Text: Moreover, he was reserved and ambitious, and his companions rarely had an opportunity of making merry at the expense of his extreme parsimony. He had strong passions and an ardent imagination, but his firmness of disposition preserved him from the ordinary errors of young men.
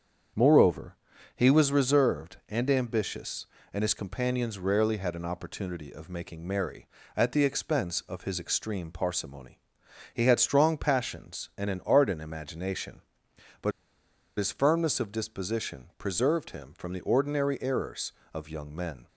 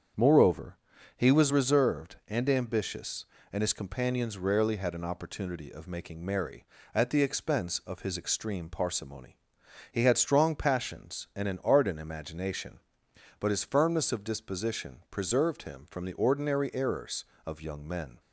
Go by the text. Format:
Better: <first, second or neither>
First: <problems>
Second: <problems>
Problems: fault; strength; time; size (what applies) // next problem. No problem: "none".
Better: second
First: starts louder than the rest; strong; until 1.7 s; 7.5 dB // pauses between "but" and "his"; noticeable; at 13.7 s; 0.67 s long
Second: starts louder than the rest; strong; until 1.5 s; 7.5 dB